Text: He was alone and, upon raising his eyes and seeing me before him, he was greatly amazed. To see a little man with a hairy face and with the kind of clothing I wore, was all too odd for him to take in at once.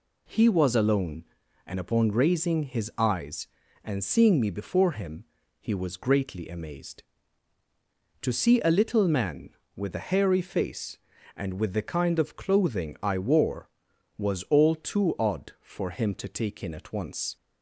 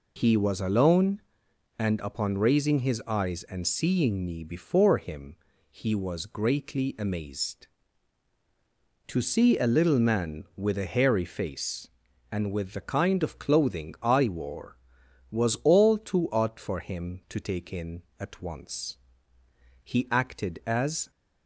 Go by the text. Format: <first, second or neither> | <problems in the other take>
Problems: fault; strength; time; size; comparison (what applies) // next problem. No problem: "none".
first | goes on to say "He acted as"; noticeable; from 19.8 s on; 1.2 s long